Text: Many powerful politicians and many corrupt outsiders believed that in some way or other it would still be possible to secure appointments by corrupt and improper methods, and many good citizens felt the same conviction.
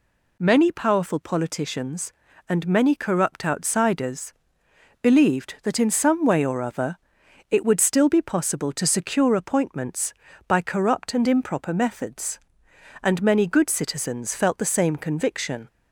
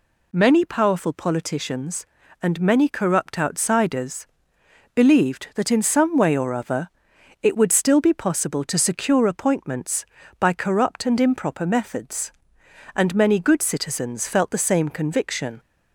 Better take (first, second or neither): neither